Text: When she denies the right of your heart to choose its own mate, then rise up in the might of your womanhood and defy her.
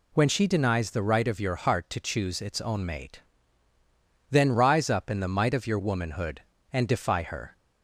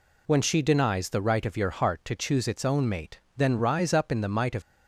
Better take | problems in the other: first | stops before "your womanhood and defy her"; at 4.6 s

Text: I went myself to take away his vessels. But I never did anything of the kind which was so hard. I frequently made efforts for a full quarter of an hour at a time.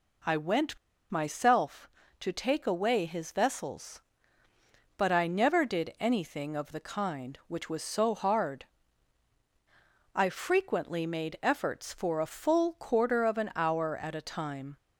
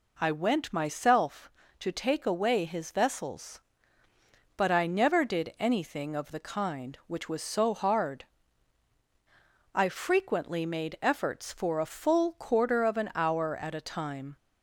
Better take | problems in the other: second | pauses between "went" and "myself"; slight; at 0.7 s; 0.32 s long

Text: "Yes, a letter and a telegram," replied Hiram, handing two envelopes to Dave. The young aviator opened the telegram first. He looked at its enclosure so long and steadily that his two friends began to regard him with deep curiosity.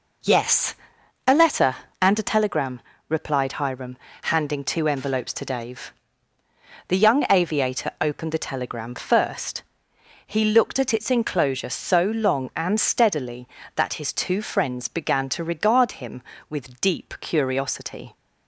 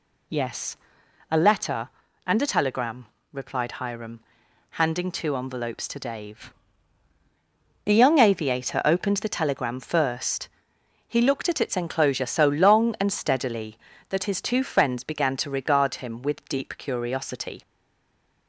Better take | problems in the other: first | stays silent after the last word; slight; from 17.6 s on; 0.8 s long

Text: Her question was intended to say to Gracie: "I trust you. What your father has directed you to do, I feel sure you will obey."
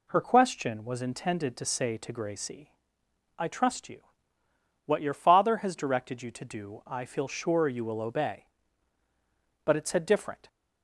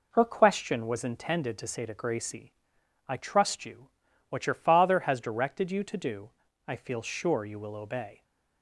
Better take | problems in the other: second | goes on to say "But it said different"; noticeable; from 9.6 s on; 0.82 s long

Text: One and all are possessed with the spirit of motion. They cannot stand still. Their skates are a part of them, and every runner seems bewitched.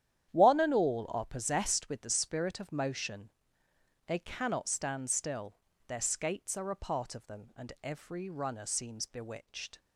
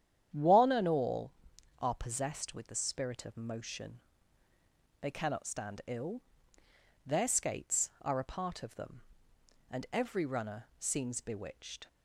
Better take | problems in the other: first | starts louder than the rest; strong; until 1.8 s; 9.5 dB; strong in the first // says "ill" for "still"; at 5.8 s

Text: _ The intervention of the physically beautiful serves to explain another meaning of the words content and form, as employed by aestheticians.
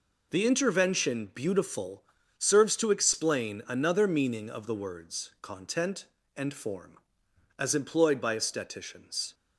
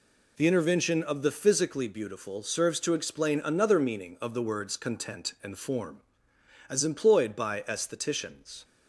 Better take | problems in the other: second | skips "of the physically"; at 1.3 s // pauses between "beautiful" and "serves"; slight; at 2.0 s; 0.34 s long

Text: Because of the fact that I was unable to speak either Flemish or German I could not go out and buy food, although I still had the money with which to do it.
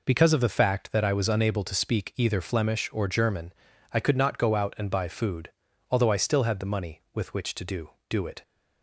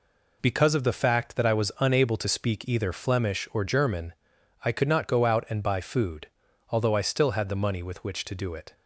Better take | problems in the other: second | pauses between "German" and "I"; at 3.5 s; 0.42 s long; noticeable in the second // says "do" twice; at 8.0 s

